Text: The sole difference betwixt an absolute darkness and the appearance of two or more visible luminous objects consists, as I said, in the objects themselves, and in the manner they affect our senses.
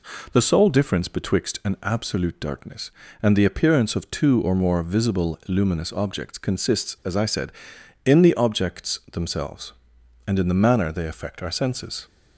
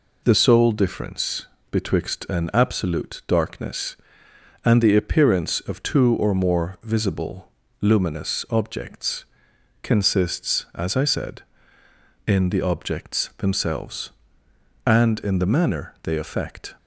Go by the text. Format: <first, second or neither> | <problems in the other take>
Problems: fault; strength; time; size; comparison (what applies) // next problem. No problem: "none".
first | pauses between "difference" and "betwixt"; slight; at 1.4 s; 0.22 s long // pauses between "visible" and "luminous"; slight; at 7.5 s; 0.30 s long // pauses between "objects" and "consists"; noticeable; at 9.2 s; 0.56 s long // stops before "our senses"; at 16.7 s